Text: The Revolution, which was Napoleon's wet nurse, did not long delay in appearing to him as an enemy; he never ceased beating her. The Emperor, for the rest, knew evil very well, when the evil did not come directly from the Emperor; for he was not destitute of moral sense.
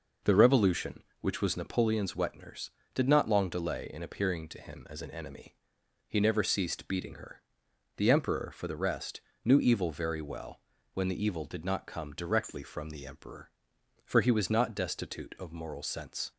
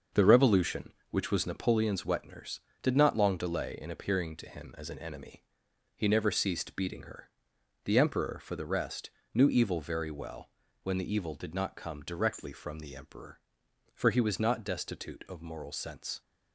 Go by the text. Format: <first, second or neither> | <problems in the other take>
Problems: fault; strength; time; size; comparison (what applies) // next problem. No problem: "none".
first | gets quieter; strong; throughout; 7 dB